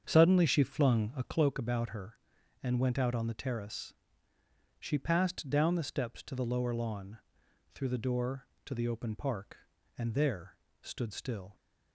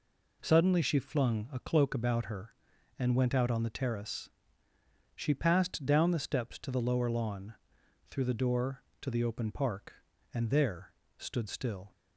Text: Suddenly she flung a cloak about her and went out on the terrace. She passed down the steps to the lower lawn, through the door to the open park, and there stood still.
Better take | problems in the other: second | starts louder than the rest; strong; until 1.4 s; 7.5 dB // pauses between "there" and "stood"; slight; at 10.5 s; 0.24 s long; slight in the second

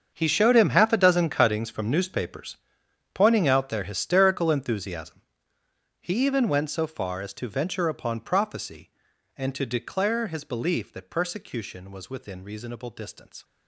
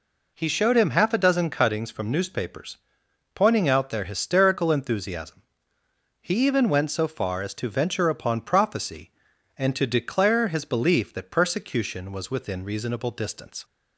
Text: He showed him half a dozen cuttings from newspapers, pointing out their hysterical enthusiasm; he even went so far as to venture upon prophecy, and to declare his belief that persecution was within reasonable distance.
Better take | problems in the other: second | gets quieter; strong; throughout; 15.5 dB

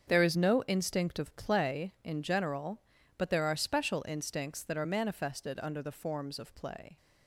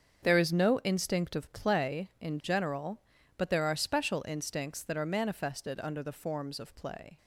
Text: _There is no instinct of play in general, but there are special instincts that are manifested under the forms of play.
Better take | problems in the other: neither | starts louder than the rest; strong; the same in both

